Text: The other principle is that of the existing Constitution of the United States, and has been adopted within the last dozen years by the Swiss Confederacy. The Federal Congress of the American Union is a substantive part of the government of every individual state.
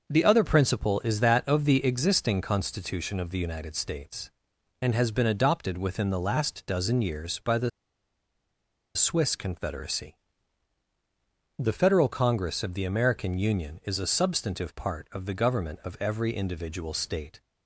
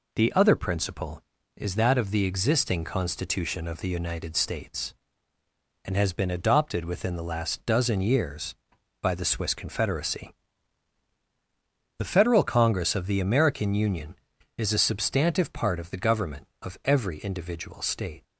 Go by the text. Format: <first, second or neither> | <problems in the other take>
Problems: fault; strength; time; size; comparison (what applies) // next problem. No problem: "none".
second | starts louder than the rest; until 1.1 s; 6 dB // pauses between "the" and "Swiss"; strong; at 7.6 s; 1.2 s long